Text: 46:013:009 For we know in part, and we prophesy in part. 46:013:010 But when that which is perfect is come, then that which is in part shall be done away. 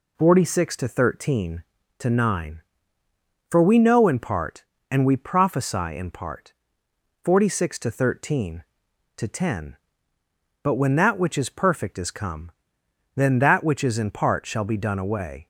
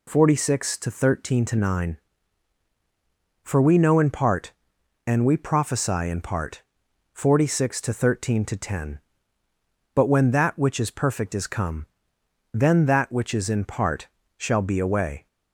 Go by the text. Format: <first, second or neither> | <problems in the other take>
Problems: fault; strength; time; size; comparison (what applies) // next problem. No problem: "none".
first | pauses between "part" and "shall"; slight; at 14.0 s; 0.30 s long // skips "done"; at 14.7 s